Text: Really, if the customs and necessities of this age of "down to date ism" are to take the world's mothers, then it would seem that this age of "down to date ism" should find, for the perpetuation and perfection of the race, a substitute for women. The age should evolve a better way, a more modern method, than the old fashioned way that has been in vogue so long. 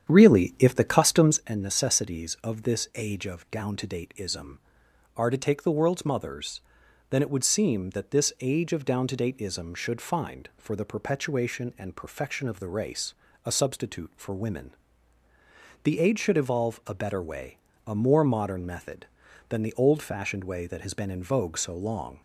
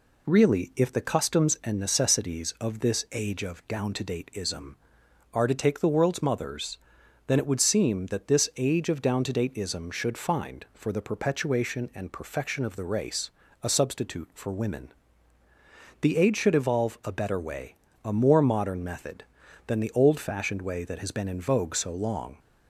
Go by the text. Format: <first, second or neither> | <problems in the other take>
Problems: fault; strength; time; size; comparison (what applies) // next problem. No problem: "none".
second | starts louder than the rest; strong; until 1.5 s; 9 dB